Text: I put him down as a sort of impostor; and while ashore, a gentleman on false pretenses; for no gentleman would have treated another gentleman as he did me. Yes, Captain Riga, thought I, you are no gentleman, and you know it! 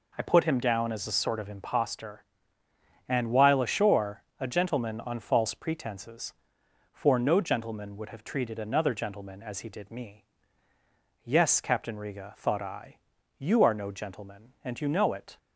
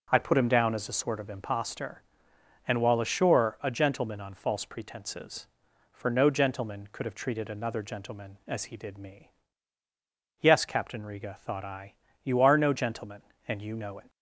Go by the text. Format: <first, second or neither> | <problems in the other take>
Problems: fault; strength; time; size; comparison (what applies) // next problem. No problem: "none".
first | says "could" for "would"; at 6.9 s